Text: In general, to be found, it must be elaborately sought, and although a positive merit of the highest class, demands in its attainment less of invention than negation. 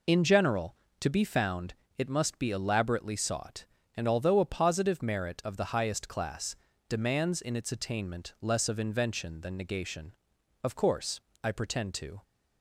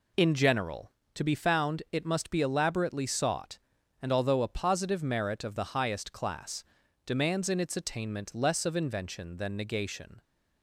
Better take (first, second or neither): second